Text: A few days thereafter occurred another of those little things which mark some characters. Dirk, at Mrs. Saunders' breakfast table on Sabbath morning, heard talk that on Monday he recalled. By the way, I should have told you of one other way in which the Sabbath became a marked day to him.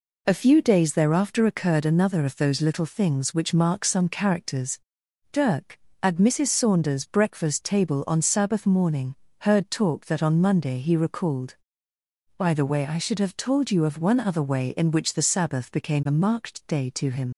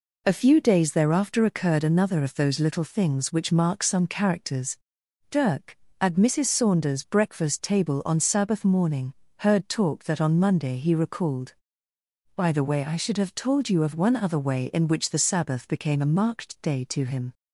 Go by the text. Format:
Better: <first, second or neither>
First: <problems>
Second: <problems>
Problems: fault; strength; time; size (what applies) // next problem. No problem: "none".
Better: second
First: leaves "him" unfinished; at 17.3 s; 60 ms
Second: none